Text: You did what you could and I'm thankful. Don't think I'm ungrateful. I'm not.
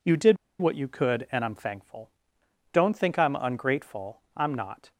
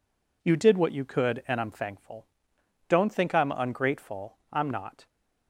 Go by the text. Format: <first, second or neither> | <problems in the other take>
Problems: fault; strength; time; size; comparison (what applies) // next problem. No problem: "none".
second | pauses between "did" and "what"; slight; at 0.3 s; 0.24 s long